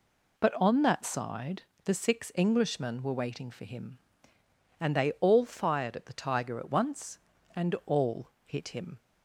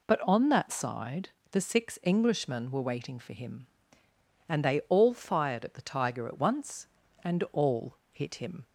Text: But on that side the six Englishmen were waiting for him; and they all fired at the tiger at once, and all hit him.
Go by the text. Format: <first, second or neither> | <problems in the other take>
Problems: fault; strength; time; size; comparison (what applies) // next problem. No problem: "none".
neither | pauses between "side" and "the"; slight; the same in both // pauses between "all" and "hit"; slight; the same in both